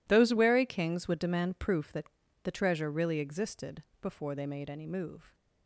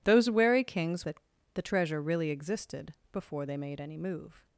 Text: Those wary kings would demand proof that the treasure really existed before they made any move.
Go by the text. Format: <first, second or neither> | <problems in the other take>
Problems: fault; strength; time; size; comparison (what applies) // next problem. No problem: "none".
first | skips "would demand proof"; at 1.0 s // pauses between "that" and "the"; slight; at 1.1 s; 0.34 s long; slight in the first // pauses between "existed" and "before"; slight; at 2.9 s; 0.18 s long; slight in the first